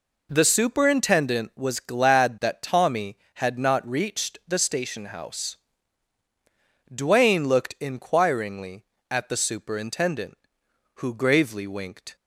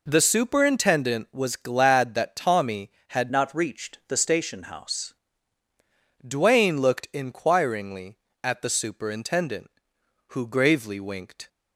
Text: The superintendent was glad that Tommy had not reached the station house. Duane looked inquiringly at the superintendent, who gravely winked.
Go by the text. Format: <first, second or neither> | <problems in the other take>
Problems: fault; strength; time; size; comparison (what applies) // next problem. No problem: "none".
first | changes voice from "not" to "house"; from 3.3 to 5.1 s; 1.8 s long